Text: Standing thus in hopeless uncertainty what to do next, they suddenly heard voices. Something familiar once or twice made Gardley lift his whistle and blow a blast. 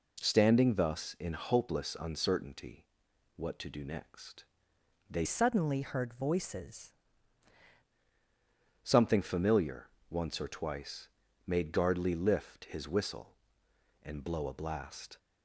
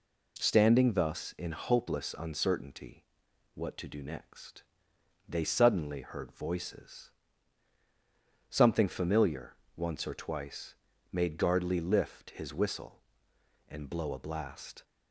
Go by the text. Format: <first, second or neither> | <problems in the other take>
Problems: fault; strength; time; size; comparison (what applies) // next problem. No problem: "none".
second | pauses between "uncertainty" and "what"; noticeable; at 2.8 s; 0.52 s long; noticeable in the second // changes voice from "suddenly" to "voices"; from 5.2 to 6.9 s; 1.7 s long // pauses between "familiar" and "once"; slight; at 9.8 s; 0.22 s long; slight in the second // pauses between "twice" and "made"; at 11.0 s; 0.38 s long; also in the second